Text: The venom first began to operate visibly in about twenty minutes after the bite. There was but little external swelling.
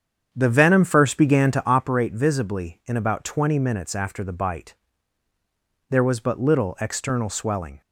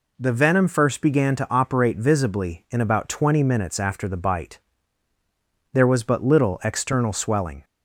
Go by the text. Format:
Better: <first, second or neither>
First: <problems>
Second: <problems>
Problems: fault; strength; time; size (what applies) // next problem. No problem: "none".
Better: second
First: starts louder than the rest; strong; until 1.9 s; 8 dB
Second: none